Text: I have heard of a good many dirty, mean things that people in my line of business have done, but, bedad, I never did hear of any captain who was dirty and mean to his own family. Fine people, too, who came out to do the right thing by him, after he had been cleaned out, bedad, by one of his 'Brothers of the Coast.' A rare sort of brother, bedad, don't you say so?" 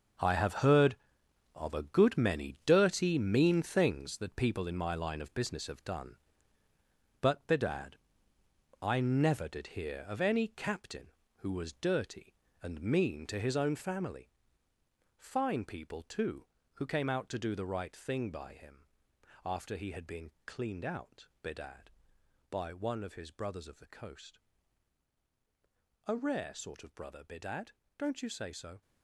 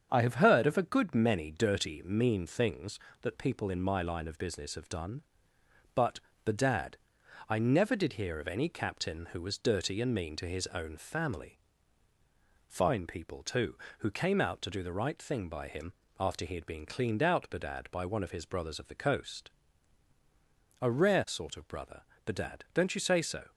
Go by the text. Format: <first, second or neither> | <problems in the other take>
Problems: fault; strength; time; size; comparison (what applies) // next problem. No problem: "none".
second | gets quieter; strong; throughout; 11.5 dB // starts louder than the rest; until 1.7 s; 6.5 dB; strong in the second // pauses between "been" and "cleaned"; slight; at 20.3 s; 0.16 s long